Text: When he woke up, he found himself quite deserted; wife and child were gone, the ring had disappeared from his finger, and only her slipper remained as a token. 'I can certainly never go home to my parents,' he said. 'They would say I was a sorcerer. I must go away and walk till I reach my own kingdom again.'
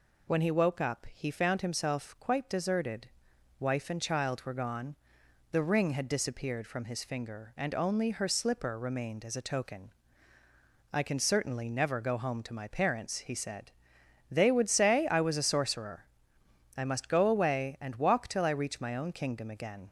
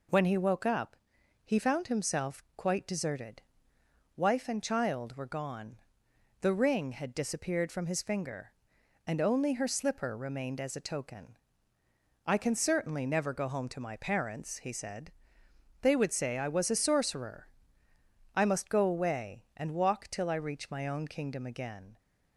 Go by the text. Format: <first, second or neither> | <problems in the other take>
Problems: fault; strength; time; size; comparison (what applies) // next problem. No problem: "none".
neither | none